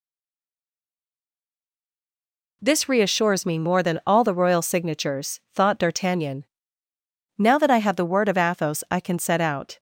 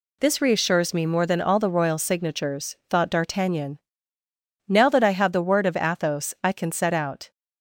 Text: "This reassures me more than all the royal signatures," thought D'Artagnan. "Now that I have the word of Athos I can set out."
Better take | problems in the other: second | stays silent before the first word; strong; until 2.6 s; 2.6 s long

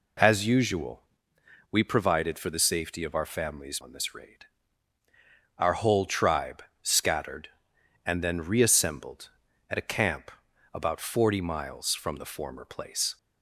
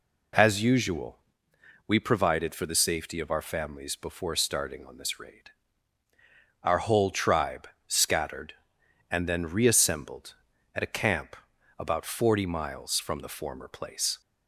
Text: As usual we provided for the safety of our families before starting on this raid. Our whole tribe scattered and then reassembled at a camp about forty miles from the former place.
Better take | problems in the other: second | pauses between "usual" and "we"; noticeable; at 1.0 s; 0.68 s long; noticeable in the second // skips "before starting"; at 3.7 s // pauses between "tribe" and "scattered"; slight; at 6.6 s; 0.18 s long; slight in the second // pauses between "camp" and "about"; at 10.3 s; 0.42 s long; also in the second

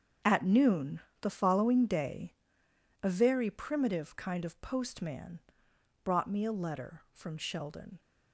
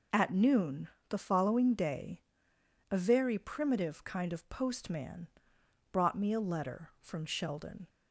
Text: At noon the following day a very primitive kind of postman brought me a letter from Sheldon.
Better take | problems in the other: second | gets quieter; strong; throughout; 13 dB // pauses between "noon" and "the"; slight; at 1.0 s; 0.22 s long; slight in the second // pauses between "day" and "a"; noticeable; at 2.3 s; 0.70 s long; noticeable in the second // pauses between "postman" and "brought"; noticeable; at 5.3 s; 0.66 s long; noticeable in the second

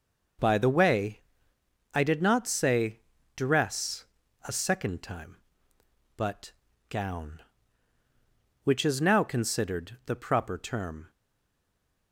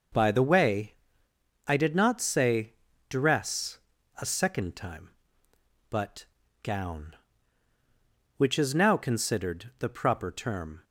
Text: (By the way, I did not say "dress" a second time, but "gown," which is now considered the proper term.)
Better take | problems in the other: second | pauses between "say" and "dress"; slight; at 2.9 s; 0.36 s long; slight in the second // pauses between "dress" and "a"; at 4.0 s; 0.42 s long; also in the second // pauses between "but" and "gown"; slight; at 6.5 s; 0.36 s long; slight in the second // stays silent after the last word; from 11.0 s on; 1.1 s long

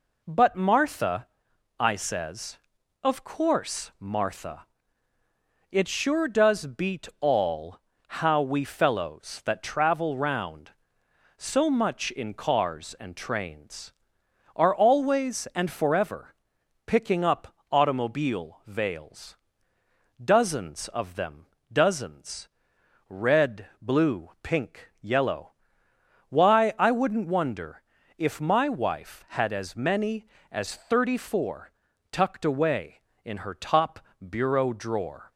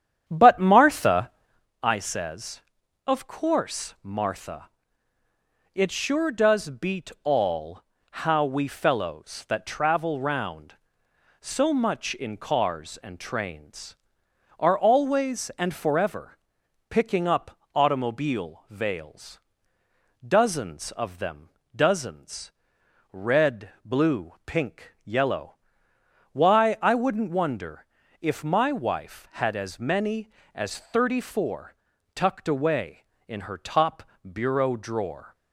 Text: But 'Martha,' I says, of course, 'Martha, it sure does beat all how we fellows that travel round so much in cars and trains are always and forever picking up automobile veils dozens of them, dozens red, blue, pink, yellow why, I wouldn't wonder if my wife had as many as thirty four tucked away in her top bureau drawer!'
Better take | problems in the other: first | starts louder than the rest; strong; until 1.7 s; 9.5 dB // pauses between "all" and "how"; at 7.8 s; 0.42 s long; also in the first // pauses between "forever" and "picking"; noticeable; at 16.3 s; 0.50 s long; noticeable in the first // pauses between "up" and "automobile"; slight; at 17.5 s; 0.18 s long; slight in the first // pauses between "veils" and "dozens"; noticeable; at 19.3 s; 0.88 s long; noticeable in the first // pauses between "dozens" and "red"; noticeable; at 22.5 s; 0.62 s long; noticeable in the first // pauses between "yellow" and "why"; noticeable; at 25.5 s; 0.78 s long; noticeable in the first // pauses between "wonder" and "if"; slight; at 27.8 s; 0.36 s long; slight in the first // pauses between "four" and "tucked"; at 31.7 s; 0.40 s long; also in the first // pauses between "top" and "bureau"; slight; at 34.0 s; 0.22 s long; slight in the first

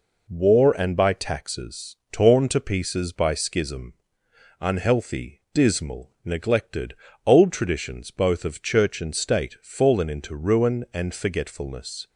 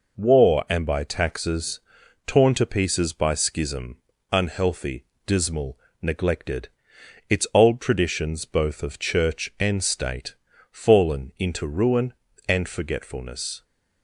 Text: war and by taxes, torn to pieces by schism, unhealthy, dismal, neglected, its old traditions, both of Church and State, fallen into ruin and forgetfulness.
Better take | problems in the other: second | skips "its"; at 7.1 s

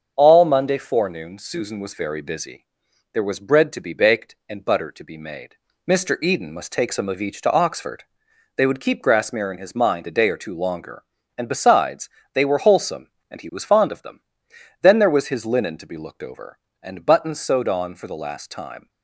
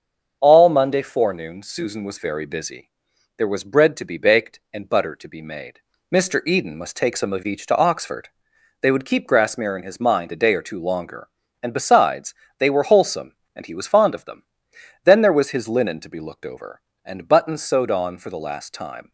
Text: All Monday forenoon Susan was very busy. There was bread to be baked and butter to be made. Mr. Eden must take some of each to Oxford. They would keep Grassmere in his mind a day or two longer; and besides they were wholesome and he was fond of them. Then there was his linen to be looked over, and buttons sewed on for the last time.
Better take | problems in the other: neither | starts louder than the rest; the same in both // pauses between "besides" and "they"; slight; the same in both

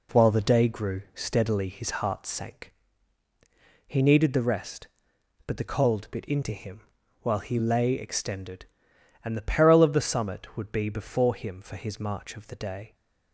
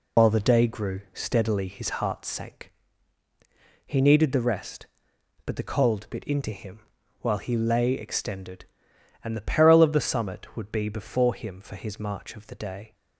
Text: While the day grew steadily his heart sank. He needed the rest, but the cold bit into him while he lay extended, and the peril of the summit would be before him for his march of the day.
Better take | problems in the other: first | loses the start of "While"; at 0.1 s; 90 ms // pauses between "him" and "while"; at 6.7 s; 0.42 s long; also in the first

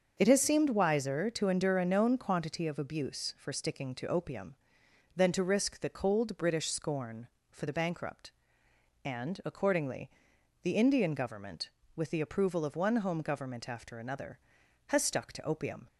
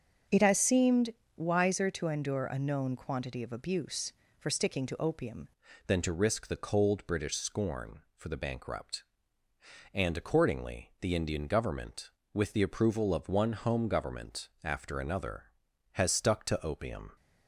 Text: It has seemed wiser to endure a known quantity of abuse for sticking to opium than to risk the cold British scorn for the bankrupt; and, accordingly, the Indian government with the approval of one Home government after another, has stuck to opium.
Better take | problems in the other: first | starts louder than the rest; until 1.5 s; 7 dB; also in the first // pauses between "seemed" and "wiser"; slight; at 1.1 s; 0.24 s long // changes voice at "than"; from 5.8 s on; 11.3 s long // pauses between "government" and "after"; slight; at 14.4 s; 0.16 s long

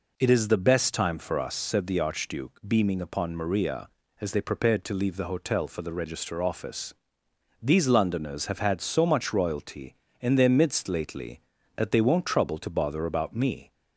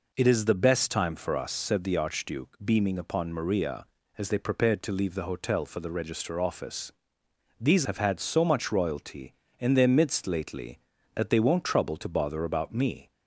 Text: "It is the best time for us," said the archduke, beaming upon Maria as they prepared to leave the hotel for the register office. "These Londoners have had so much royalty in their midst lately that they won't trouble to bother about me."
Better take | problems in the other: first | skips "Londoners"; at 7.8 s

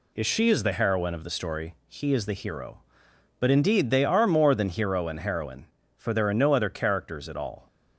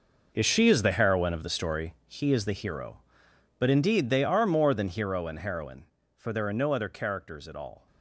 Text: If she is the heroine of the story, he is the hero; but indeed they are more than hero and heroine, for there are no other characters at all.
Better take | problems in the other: first | gets quieter; strong; throughout; 12 dB

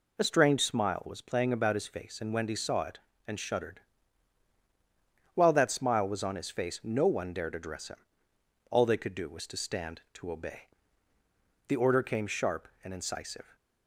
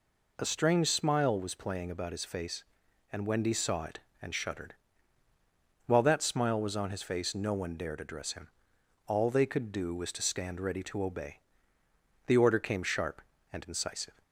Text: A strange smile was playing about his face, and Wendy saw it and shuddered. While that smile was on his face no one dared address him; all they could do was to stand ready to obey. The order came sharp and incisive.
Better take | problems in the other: second | skips "ready"; at 10.0 s

